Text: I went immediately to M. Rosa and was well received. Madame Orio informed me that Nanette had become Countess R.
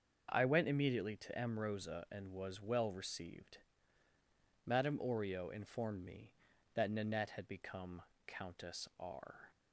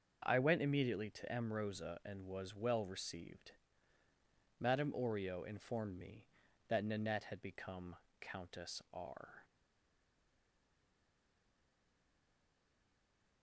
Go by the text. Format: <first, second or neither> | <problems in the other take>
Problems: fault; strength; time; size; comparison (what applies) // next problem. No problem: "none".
first | starts louder than the rest; until 1.2 s; 6.5 dB; also in the first // pauses between "become" and "Countess"; slight; at 7.9 s; 0.24 s long; slight in the first // stays silent after the last word; strong; from 9.4 s on; 4.0 s long